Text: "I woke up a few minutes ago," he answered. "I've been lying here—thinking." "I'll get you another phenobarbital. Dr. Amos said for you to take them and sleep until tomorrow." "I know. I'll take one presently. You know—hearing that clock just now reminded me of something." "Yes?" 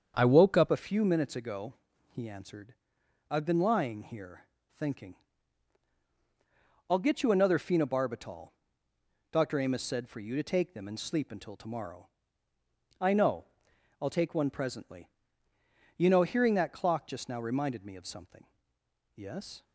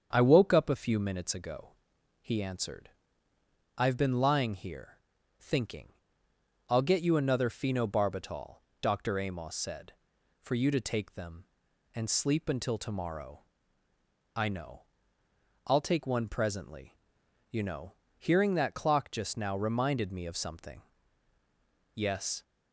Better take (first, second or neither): second